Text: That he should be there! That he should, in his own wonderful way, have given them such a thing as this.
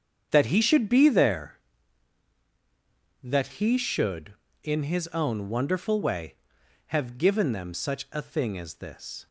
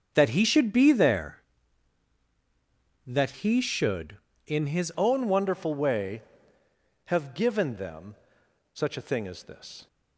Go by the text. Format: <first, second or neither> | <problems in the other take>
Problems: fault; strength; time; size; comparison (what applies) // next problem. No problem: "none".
first | starts louder than the rest; strong; until 1.1 s; 7.5 dB; strong in the first // changes voice at "own"; from 4.9 s on; 4.9 s long // pauses between "them" and "such"; noticeable; at 8.1 s; 0.58 s long